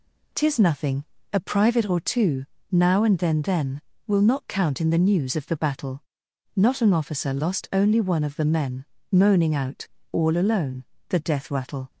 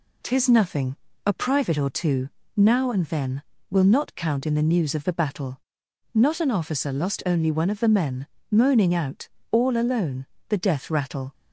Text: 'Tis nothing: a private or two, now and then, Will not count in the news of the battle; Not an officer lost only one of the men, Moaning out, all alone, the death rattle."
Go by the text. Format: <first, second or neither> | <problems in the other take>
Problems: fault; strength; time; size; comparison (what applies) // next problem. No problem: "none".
second | says "then" twice; at 3.4 s